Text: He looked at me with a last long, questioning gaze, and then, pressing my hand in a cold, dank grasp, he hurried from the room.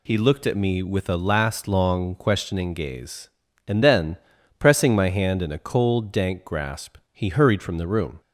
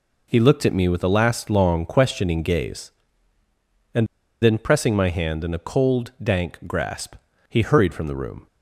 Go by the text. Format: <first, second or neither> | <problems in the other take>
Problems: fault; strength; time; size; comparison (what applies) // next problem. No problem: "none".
first | pauses between "and" and "then"; slight; at 4.0 s; 0.35 s long